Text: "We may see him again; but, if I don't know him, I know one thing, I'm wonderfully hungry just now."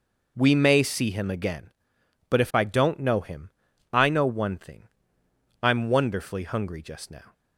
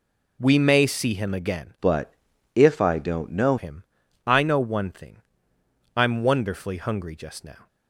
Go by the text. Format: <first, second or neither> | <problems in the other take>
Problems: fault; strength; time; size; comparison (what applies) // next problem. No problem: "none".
first | changes voice from "but" to "know"; from 1.8 to 3.5 s; 1.7 s long